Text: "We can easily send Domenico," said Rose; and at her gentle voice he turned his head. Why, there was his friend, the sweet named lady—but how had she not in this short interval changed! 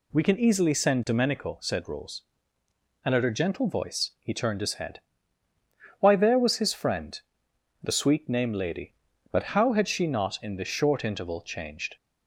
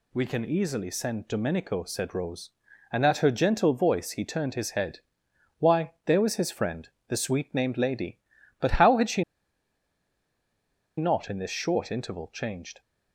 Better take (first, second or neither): first